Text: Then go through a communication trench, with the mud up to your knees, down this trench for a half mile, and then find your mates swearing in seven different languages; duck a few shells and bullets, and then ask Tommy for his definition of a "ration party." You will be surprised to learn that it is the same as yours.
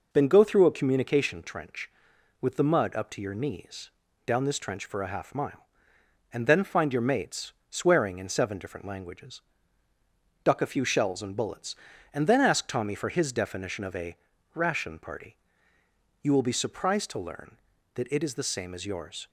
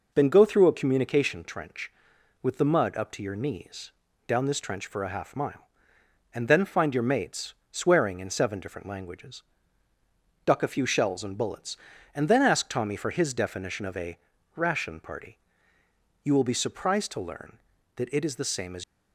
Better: first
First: pauses between "mates" and "swearing"; slight; at 7.5 s; 0.16 s long // pauses between "a" and "ration"; slight; at 14.1 s; 0.36 s long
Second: pauses between "mates" and "swearing"; slight; at 7.5 s; 0.16 s long // pauses between "a" and "ration"; slight; at 14.1 s; 0.36 s long // stops before "yours"; at 18.8 s

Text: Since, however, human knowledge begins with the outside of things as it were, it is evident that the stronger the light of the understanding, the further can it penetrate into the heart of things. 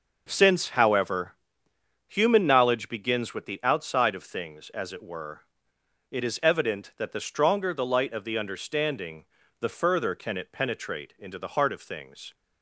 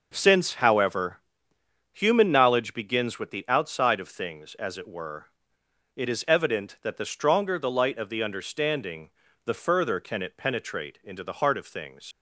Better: first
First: none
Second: leaves "things" unfinished; at 12.1 s; 70 ms

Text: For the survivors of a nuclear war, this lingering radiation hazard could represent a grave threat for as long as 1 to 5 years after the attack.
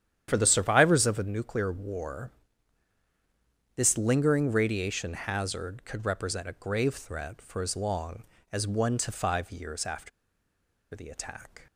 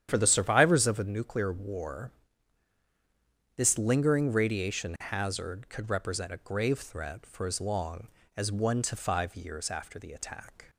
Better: second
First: starts louder than the rest; strong; until 1.3 s; 10 dB // pauses between "after" and "the"; noticeable; at 10.1 s; 0.84 s long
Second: starts louder than the rest; strong; until 1.1 s; 10 dB

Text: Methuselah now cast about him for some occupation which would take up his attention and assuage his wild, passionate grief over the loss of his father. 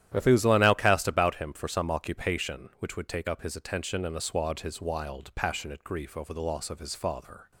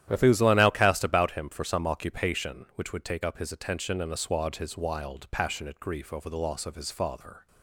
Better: neither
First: starts louder than the rest; strong; until 1.1 s; 11.5 dB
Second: starts louder than the rest; strong; until 1.0 s; 11.5 dB

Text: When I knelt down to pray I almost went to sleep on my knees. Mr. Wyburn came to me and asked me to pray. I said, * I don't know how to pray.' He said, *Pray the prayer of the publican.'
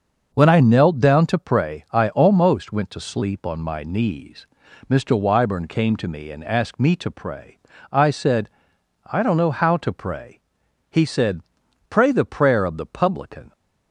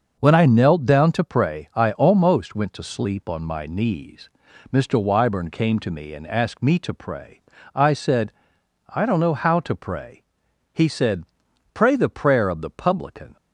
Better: neither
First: starts louder than the rest; until 1.3 s; 6.5 dB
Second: starts louder than the rest; noticeable; until 1.1 s; 6 dB

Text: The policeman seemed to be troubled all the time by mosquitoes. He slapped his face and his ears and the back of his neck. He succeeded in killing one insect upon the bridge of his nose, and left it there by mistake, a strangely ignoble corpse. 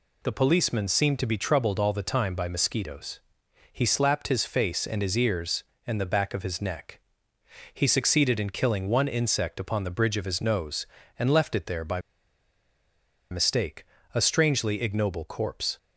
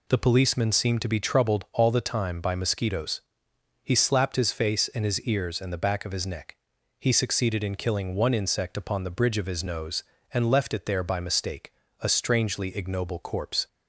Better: second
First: pauses between "by" and "mistake"; strong; at 11.9 s; 1.3 s long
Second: none

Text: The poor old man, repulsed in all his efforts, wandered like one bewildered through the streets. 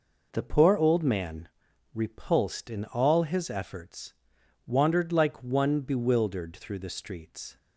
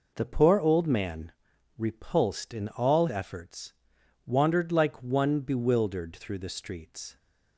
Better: first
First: none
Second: skips "his"; at 3.0 s

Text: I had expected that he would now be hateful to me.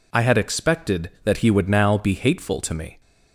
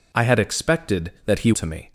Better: first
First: none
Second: skips "would now be hateful"; at 1.5 s

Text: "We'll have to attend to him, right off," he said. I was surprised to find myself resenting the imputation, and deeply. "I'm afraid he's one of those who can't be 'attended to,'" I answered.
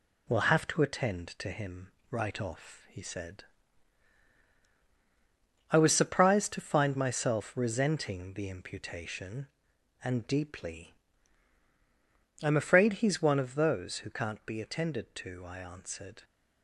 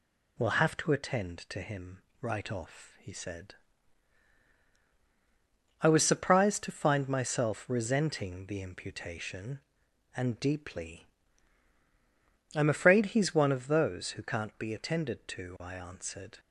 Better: second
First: gets quieter; throughout; 4 dB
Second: none

